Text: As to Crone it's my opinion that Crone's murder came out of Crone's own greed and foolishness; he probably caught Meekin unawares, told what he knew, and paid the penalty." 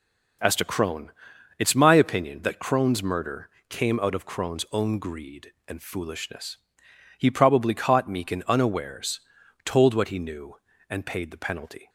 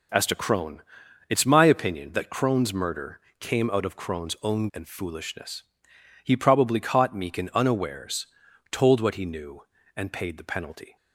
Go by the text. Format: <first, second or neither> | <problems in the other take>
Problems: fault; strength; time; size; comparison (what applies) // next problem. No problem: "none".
first | pauses between "Crone" and "it's"; noticeable; at 0.8 s; 0.46 s long; noticeable in the first // pauses between "murder" and "came"; slight; at 3.2 s; 0.18 s long; slight in the first // skips "greed"; at 4.7 s